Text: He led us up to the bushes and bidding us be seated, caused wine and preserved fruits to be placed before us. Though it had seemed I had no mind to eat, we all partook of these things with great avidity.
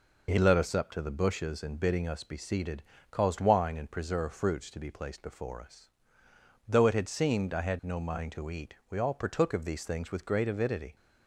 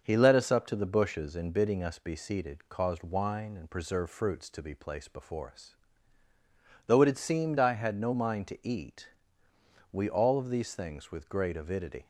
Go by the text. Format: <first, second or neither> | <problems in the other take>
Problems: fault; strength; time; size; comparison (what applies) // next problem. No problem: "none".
first | starts louder than the rest; until 1.0 s; 6.5 dB // skips "partook"; at 10.3 s